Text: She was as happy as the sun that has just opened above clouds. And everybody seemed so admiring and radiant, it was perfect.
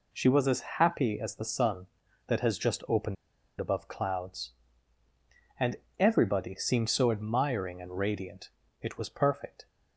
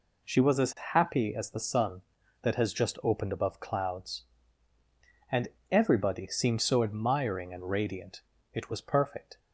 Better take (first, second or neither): second